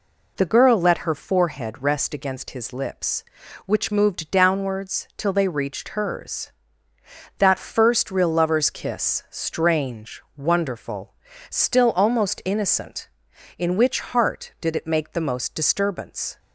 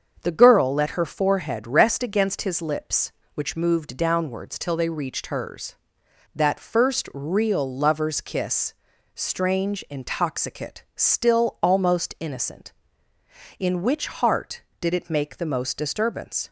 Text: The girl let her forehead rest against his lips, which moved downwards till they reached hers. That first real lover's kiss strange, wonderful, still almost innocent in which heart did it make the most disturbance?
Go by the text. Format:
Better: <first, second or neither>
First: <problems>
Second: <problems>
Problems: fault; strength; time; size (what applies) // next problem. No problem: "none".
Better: first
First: none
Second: starts louder than the rest; until 1.2 s; 7 dB // pauses between "kiss" and "strange"; at 8.7 s; 0.40 s long // says "intoxicate" for "wonderful"; at 9.8 s